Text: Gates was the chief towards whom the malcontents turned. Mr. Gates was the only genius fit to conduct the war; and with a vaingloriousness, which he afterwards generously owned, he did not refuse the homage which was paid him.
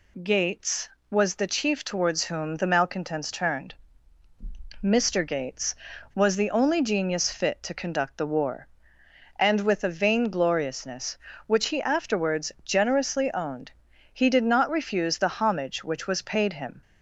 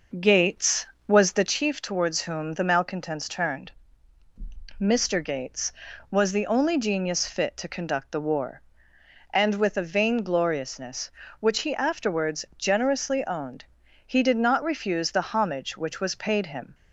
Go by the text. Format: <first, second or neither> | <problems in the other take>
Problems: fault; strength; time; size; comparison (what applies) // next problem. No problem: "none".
first | starts louder than the rest; noticeable; until 1.5 s; 5.5 dB